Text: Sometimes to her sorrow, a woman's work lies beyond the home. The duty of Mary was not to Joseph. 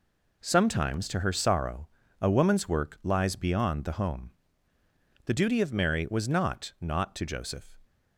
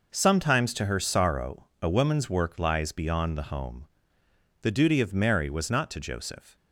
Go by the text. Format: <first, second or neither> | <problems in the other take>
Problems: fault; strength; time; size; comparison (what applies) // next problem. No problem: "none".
second | says "not" twice; at 6.8 s